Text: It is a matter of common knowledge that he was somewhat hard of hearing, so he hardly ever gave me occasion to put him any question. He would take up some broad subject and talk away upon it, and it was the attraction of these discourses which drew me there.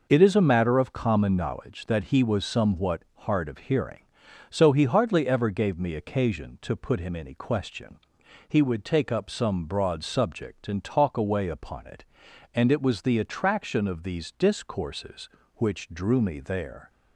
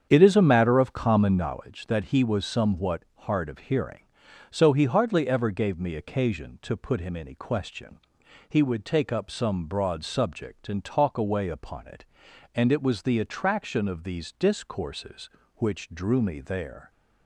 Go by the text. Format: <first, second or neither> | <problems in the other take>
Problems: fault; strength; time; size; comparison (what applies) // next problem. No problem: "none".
first | starts louder than the rest; strong; until 1.5 s; 8 dB // pauses between "somewhat" and "hard"; slight; at 3.0 s; 0.16 s long; slight in the first